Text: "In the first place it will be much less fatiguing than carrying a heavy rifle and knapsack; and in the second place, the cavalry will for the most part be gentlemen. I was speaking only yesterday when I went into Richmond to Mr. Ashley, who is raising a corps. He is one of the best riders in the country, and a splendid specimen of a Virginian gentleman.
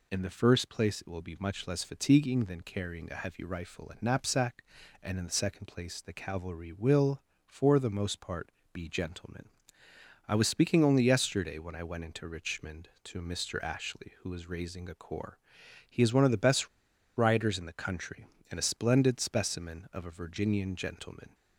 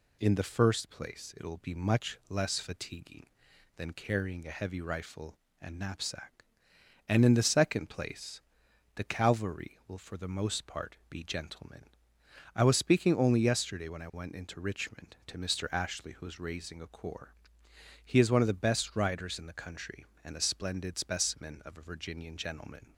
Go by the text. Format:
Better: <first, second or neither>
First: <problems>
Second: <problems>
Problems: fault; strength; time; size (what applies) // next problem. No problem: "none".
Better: second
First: pauses between "part" and "be"; slight; at 8.5 s; 0.20 s long // pauses between "best" and "riders"; noticeable; at 16.6 s; 0.49 s long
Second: none